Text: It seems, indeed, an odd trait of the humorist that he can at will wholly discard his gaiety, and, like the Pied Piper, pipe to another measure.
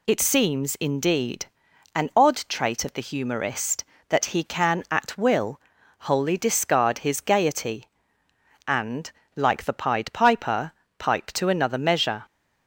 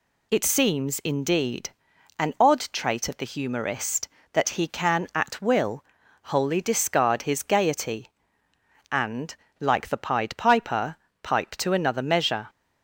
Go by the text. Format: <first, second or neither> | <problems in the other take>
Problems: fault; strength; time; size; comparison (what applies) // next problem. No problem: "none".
neither | pauses between "will" and "wholly"; the same in both